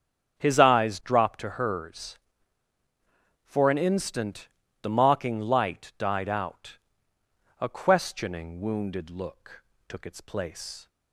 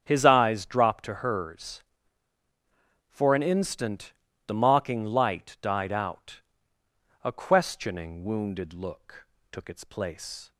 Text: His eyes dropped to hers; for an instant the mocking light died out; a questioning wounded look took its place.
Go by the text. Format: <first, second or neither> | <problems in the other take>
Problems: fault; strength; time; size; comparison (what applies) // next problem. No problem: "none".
neither | starts louder than the rest; strong; the same in both // pauses between "instant" and "the"; slight; the same in both // pauses between "look" and "took"; slight; the same in both